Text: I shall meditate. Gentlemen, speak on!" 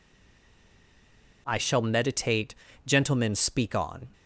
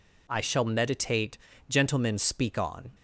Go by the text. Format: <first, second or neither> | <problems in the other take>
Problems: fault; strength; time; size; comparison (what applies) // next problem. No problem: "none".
second | stays silent before the first word; noticeable; until 1.4 s; 1.4 s long